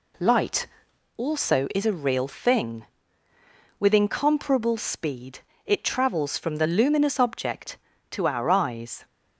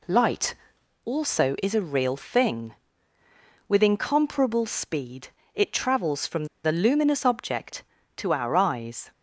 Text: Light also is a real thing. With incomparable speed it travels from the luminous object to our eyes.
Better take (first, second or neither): first